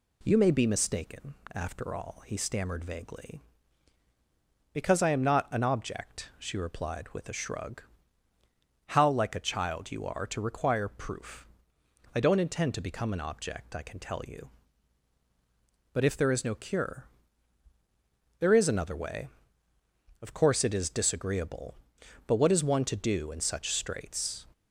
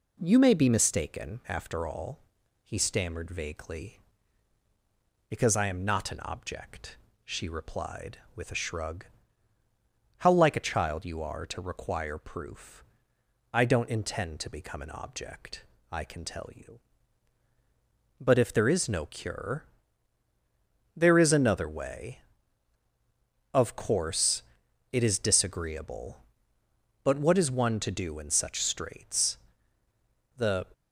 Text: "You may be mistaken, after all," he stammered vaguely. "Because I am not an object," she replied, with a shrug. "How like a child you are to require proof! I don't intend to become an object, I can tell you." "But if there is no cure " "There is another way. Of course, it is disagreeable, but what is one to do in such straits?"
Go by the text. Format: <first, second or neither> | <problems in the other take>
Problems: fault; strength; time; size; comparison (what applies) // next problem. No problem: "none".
first | goes on to say "The"; slight; from 30.3 s on; 0.32 s long